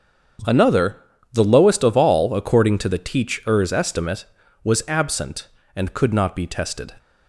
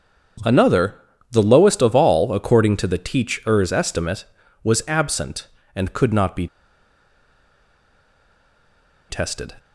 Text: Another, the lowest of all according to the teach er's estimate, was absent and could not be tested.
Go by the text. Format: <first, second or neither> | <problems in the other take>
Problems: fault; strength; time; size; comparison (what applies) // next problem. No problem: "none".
first | starts louder than the rest; strong; until 1.8 s; 7.5 dB; strong in the first // pauses between "be" and "tested"; strong; at 6.4 s; 2.6 s long